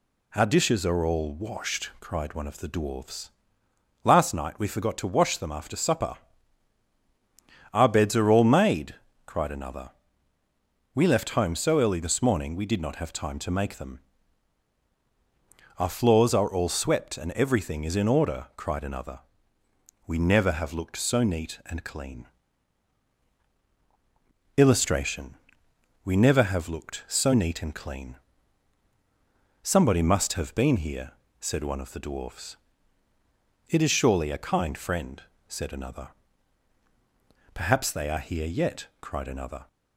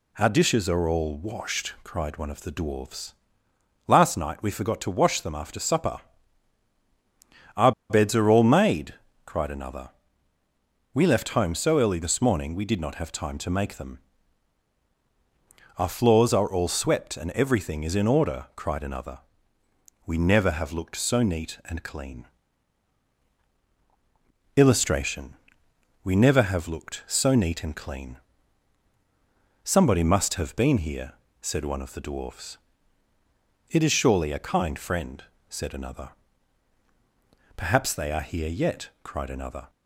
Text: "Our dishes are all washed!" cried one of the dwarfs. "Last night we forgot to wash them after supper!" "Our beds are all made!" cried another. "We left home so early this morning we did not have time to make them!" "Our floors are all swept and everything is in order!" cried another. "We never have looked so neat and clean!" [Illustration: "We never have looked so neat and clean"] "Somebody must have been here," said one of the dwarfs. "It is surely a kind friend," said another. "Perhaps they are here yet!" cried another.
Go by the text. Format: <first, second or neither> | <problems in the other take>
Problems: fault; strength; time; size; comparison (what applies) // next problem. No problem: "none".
first | pauses between "Our" and "beds"; slight; at 7.7 s; 0.18 s long // pauses between "clean" and "Somebody"; strong; at 28.1 s; 1.4 s long; strong in the first